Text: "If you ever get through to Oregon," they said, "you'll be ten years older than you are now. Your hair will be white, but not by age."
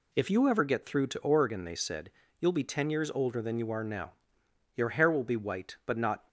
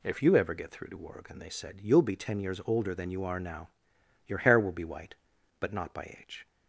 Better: second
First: stops before "by age"; at 6.2 s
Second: none

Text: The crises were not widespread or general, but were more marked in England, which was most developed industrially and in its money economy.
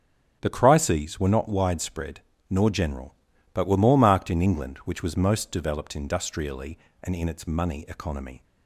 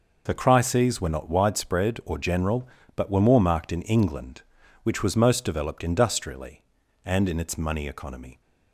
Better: second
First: starts louder than the rest; strong; until 1.4 s; 7.5 dB // says "nor" for "or"; at 2.4 s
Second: none

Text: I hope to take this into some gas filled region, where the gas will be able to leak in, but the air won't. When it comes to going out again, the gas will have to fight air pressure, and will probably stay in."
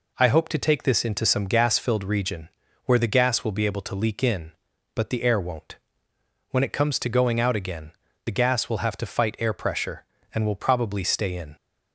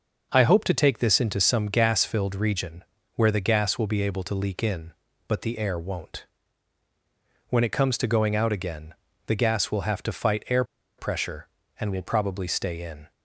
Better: first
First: none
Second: starts louder than the rest; noticeable; until 1.3 s; 6 dB // pauses between "air" and "pressure"; slight; at 10.6 s; 0.34 s long

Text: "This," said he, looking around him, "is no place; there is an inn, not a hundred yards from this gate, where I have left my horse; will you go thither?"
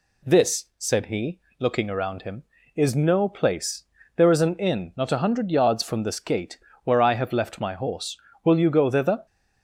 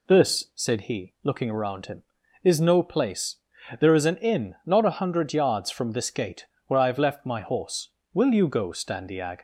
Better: first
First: none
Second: says "standiag" for "thither"; at 8.6 s

